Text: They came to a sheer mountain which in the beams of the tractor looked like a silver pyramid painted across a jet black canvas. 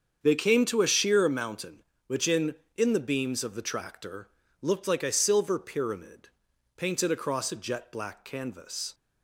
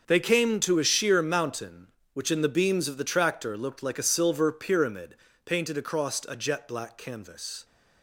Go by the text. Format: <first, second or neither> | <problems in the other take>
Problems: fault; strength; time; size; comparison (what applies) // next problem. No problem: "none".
second | starts louder than the rest; strong; until 1.2 s; 7 dB; also in the second // says "in" twice; at 2.7 s // pauses between "tractor" and "looked"; slight; at 4.2 s; 0.32 s long // pauses between "pyramid" and "painted"; noticeable; at 6.2 s; 0.48 s long; slight in the second